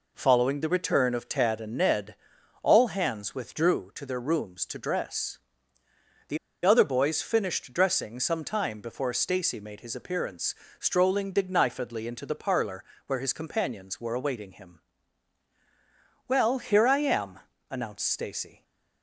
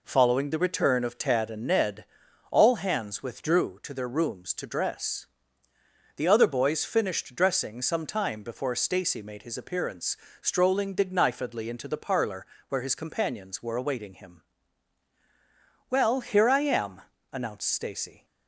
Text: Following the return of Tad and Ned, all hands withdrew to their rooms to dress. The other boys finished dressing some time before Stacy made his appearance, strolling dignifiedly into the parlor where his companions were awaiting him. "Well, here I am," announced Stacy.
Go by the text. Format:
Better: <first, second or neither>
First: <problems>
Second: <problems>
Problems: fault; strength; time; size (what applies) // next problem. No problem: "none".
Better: second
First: pauses between "The" and "other"; slight; at 6.3 s; 0.27 s long // pauses between "parlor" and "where"; slight; at 12.8 s; 0.22 s long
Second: pauses between "parlor" and "where"; slight; at 12.4 s; 0.22 s long